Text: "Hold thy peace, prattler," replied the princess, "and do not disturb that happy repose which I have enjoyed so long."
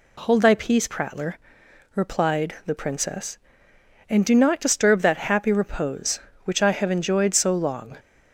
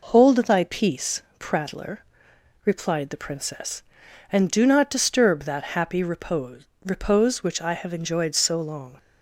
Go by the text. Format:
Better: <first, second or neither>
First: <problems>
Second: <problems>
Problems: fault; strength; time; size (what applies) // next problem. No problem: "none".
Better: first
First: none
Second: says "repose" twice; at 6.8 s